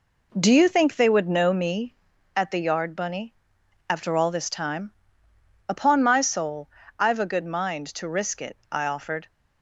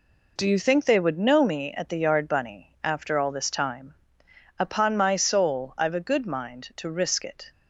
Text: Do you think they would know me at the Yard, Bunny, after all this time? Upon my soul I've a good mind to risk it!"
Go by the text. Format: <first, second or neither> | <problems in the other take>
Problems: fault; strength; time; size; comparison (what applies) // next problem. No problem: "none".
second | pauses between "soul" and "I've"; slight; at 6.6 s; 0.30 s long // goes on to say "I offered"; from 8.6 s on; 0.60 s long